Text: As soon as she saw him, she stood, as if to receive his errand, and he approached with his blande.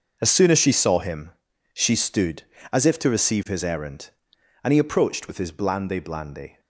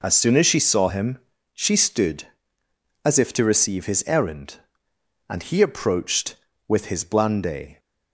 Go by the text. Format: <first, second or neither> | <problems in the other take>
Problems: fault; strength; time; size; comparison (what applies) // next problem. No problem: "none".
second | says "blande" twice; at 6.0 s